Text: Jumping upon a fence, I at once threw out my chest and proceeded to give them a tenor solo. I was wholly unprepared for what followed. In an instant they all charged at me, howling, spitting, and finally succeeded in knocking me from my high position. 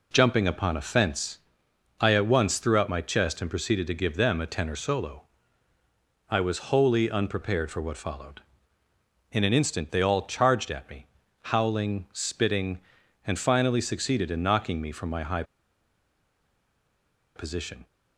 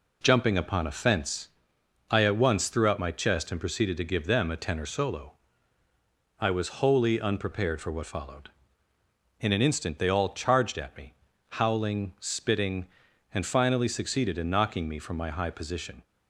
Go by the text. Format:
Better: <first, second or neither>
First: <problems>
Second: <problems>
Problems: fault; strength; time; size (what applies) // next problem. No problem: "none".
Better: second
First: pauses between "high" and "position"; strong; at 15.4 s; 1.9 s long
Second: none